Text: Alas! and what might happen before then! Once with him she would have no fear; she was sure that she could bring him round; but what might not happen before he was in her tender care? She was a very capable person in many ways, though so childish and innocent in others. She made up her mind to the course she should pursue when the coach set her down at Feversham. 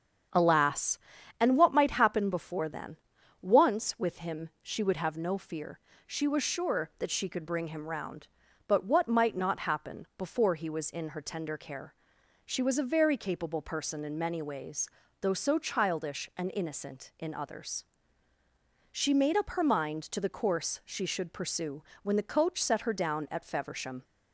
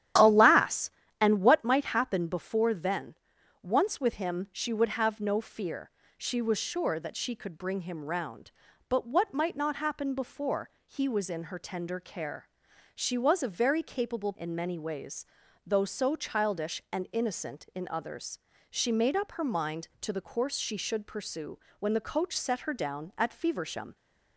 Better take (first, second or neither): first